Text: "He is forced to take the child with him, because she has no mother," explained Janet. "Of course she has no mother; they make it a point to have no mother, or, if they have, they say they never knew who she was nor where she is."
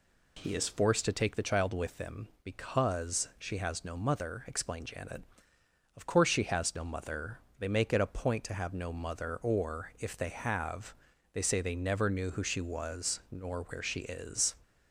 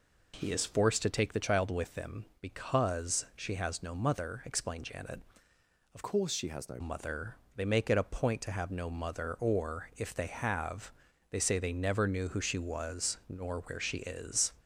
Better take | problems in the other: first | changes voice from "course" to "no"; from 6.0 to 6.8 s; 0.8 s long

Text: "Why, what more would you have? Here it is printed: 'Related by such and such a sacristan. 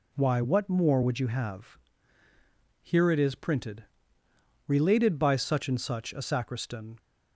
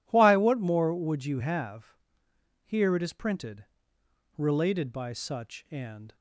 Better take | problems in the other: first | stops before "such a sacristan"; at 6.1 s

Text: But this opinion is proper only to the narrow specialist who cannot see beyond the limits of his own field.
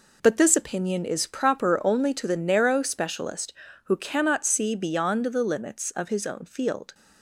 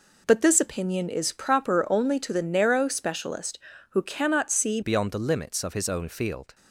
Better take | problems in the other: first | changes voice at "beyond"; from 4.8 s on; 1.7 s long

